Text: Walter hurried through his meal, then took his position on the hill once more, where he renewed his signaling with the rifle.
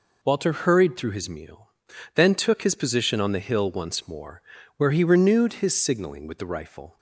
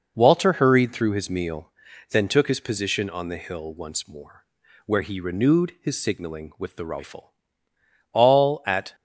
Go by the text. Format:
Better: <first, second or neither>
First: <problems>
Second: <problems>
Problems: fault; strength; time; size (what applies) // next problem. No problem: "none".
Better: first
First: none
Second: goes on to say "All at"; noticeable; from 8.1 s on; 0.82 s long